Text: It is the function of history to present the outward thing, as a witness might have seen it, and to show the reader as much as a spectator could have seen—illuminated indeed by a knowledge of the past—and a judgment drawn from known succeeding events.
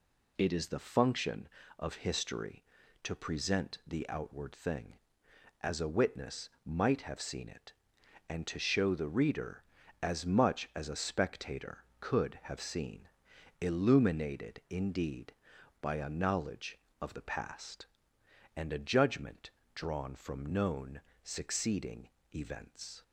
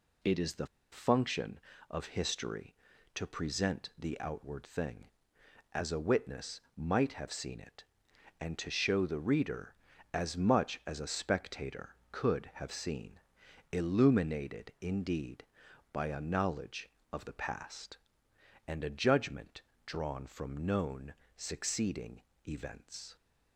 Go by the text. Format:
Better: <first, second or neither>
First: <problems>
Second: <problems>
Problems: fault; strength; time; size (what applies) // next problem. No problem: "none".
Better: first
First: pauses between "witness" and "might"; slight; at 6.4 s; 0.16 s long // pauses between "judgment" and "drawn"; slight; at 19.5 s; 0.24 s long // pauses between "known" and "succeeding"; slight; at 21.0 s; 0.22 s long // pauses between "succeeding" and "events"; slight; at 22.0 s; 0.26 s long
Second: pauses between "the" and "function"; slight; at 0.6 s; 0.26 s long // pauses between "witness" and "might"; slight; at 6.5 s; 0.16 s long // pauses between "judgment" and "drawn"; slight; at 19.6 s; 0.24 s long // pauses between "known" and "succeeding"; slight; at 21.1 s; 0.22 s long // pauses between "succeeding" and "events"; slight; at 22.2 s; 0.26 s long